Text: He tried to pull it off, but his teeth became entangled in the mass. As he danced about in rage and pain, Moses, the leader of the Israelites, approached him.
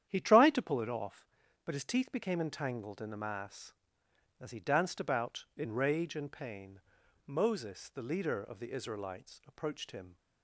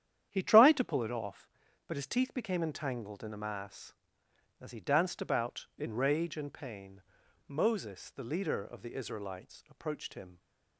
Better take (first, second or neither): neither